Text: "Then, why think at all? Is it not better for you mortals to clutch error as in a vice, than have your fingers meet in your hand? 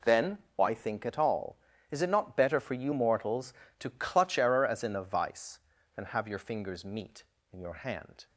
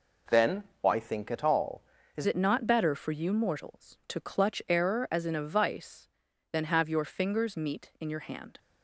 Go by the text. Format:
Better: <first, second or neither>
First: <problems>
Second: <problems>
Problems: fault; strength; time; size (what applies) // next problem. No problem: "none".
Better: first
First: none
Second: changes voice at "it"; from 2.2 s on; 6.3 s long